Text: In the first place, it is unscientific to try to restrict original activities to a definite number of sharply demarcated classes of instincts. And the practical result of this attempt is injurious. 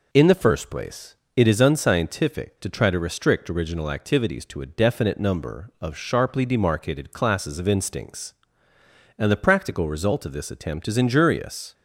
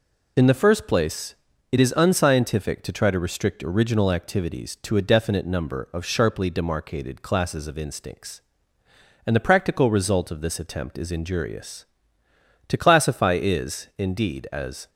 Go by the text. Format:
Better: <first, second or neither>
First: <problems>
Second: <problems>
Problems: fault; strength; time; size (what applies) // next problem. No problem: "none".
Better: first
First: none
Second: goes on to say "To classify is indeed as"; strong; from 12.6 s on; 2.2 s long